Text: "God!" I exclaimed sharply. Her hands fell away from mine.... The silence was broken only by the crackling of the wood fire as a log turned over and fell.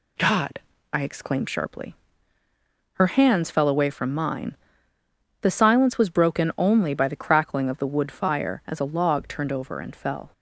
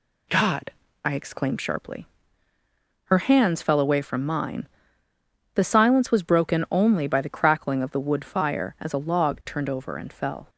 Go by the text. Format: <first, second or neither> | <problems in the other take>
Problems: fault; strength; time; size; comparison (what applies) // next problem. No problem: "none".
neither | none